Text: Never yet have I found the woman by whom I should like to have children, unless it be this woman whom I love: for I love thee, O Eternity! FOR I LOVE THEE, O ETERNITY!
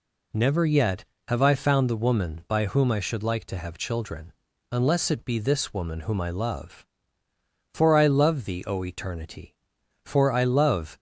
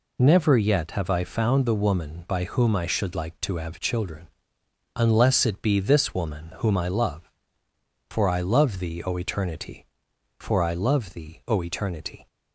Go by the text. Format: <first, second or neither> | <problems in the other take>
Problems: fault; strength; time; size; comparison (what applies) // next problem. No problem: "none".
second | stops before "THEE O ETERNITY"; at 10.9 s